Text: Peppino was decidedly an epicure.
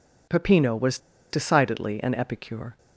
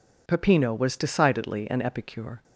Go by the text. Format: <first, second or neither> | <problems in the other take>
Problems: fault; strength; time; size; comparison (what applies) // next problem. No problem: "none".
second | pauses between "was" and "decidedly"; slight; at 0.9 s; 0.32 s long